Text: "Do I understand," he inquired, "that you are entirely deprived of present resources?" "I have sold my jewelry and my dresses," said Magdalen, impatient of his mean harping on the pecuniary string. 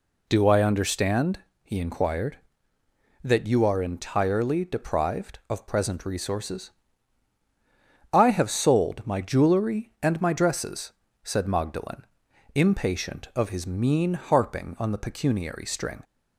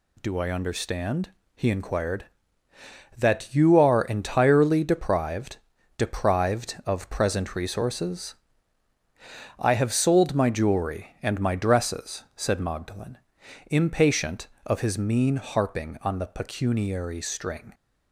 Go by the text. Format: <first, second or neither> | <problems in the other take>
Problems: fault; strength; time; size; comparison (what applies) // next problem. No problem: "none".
first | says "deprived" twice; at 5.9 s